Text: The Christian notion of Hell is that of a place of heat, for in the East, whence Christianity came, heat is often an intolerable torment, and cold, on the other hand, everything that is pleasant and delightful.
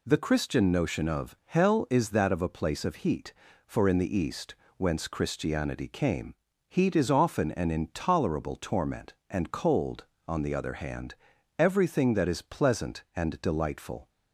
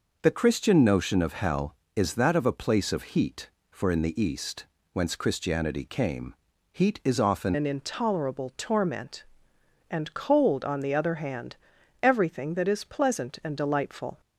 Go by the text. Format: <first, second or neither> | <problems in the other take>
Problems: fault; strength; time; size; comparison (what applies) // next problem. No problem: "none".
first | changes voice at "an"; from 7.5 s on; 6.7 s long